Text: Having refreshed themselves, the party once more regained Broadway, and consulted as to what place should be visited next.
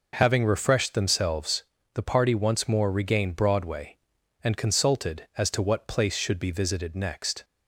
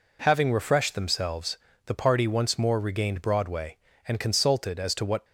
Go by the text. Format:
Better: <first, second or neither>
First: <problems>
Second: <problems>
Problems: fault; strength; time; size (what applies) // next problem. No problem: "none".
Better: first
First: none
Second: stops before "place should be visited next"; at 5.2 s